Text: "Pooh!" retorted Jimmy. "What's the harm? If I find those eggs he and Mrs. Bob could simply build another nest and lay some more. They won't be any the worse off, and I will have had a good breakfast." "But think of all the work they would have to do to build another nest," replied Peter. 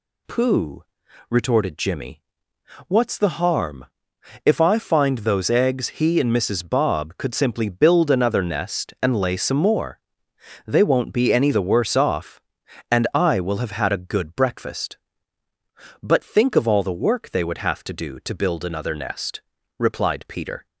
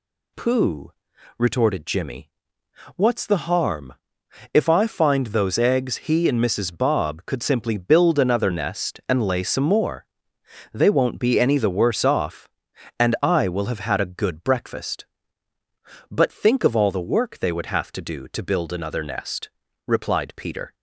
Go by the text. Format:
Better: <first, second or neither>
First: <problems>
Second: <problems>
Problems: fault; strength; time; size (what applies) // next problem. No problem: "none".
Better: neither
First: none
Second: none